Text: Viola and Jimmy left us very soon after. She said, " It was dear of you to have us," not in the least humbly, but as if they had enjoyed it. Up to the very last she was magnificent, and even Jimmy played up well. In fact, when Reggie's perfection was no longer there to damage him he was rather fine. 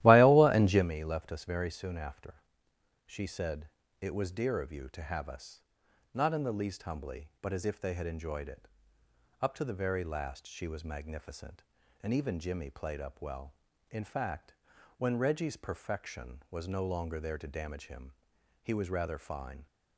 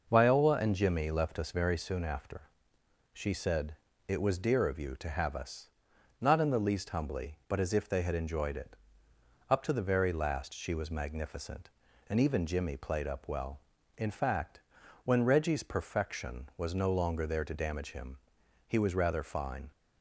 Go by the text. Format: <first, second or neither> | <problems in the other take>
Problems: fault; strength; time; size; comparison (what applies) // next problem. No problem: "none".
second | starts louder than the rest; strong; until 0.9 s; 14.5 dB // pauses between "him" and "he"; noticeable; at 18.1 s; 0.50 s long; noticeable in the second